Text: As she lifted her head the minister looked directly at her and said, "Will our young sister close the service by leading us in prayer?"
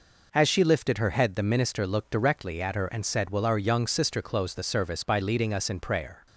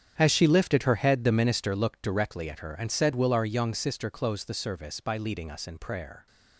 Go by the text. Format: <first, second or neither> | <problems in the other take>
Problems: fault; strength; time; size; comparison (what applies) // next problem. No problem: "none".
first | gets quieter; strong; throughout; 14 dB